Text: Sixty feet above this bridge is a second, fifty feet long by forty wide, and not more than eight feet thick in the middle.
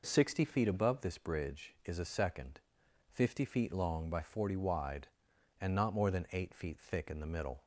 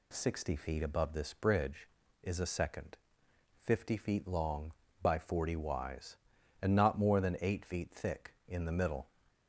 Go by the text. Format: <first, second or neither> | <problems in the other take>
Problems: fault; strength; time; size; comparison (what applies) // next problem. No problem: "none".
first | says "wise" for "wide"; at 5.5 s